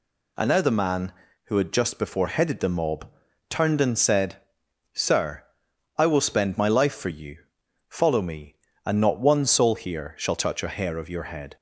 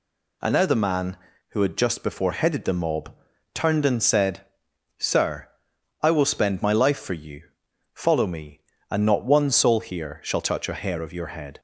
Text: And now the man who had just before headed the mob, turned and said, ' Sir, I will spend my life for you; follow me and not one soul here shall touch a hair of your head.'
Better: neither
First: none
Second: none

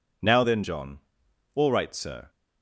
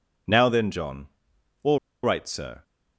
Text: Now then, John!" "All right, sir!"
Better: first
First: none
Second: pauses between "All" and "right"; slight; at 1.7 s; 0.25 s long

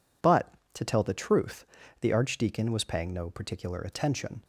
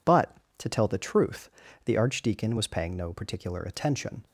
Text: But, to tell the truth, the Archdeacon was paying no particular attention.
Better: neither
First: none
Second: none

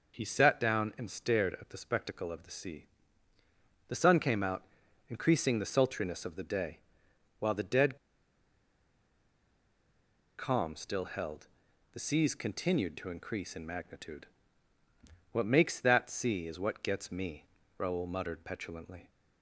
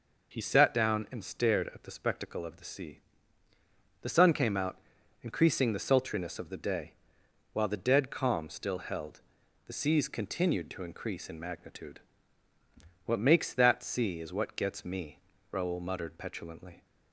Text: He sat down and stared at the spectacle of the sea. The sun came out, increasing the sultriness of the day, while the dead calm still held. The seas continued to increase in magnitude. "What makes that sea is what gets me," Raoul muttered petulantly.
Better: second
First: pauses between "dead" and "calm"; strong; at 7.9 s; 2.4 s long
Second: none

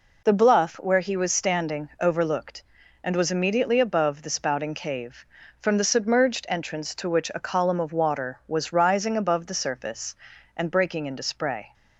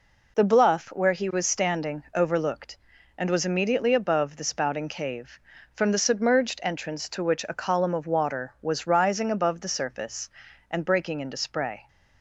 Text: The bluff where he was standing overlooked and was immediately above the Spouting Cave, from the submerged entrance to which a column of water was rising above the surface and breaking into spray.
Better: neither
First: none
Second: none

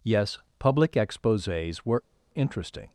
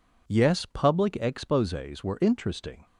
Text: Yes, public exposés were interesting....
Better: second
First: pauses between "were" and "interesting"; slight; at 2.0 s; 0.33 s long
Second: none

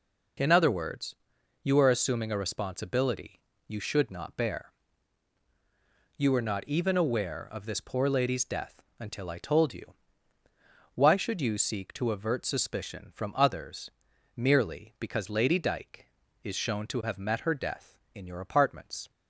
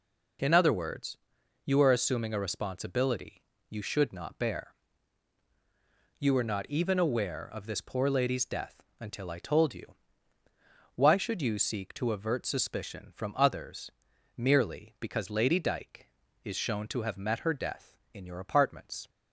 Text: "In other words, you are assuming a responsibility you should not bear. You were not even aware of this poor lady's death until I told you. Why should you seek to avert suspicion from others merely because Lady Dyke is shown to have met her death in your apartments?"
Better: neither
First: pauses between "responsibility" and "you"; slight; at 3.4 s; 0.26 s long // pauses between "death" and "until"; slight; at 8.8 s; 0.20 s long // pauses between "others" and "merely"; noticeable; at 13.9 s; 0.46 s long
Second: pauses between "responsibility" and "you"; slight; at 3.4 s; 0.26 s long // pauses between "death" and "until"; slight; at 8.8 s; 0.20 s long // pauses between "others" and "merely"; noticeable; at 13.9 s; 0.46 s long

